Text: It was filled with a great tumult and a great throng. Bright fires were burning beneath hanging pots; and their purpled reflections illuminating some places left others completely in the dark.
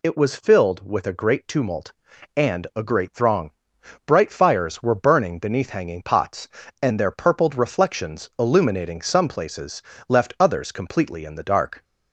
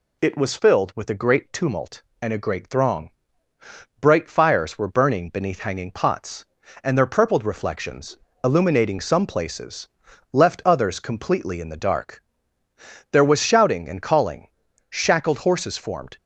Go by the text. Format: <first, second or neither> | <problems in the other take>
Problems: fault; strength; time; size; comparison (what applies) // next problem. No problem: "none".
first | pauses between "reflections" and "illuminating"; slight; at 8.1 s; 0.26 s long // pauses between "places" and "left"; noticeable; at 9.8 s; 0.46 s long; slight in the first // goes on to say "There was shouting and calling shackled horses formed"; strong; from 13.1 s on; 3.0 s long